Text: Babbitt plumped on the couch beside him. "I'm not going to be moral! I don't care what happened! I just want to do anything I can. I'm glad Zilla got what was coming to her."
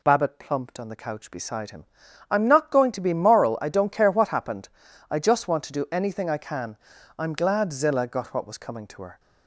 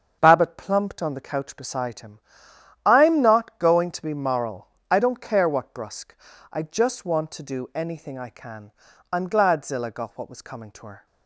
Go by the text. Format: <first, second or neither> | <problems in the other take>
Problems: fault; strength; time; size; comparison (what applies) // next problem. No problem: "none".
first | starts louder than the rest; until 1.2 s; 7 dB // says "brusque" for "happened"; at 5.7 s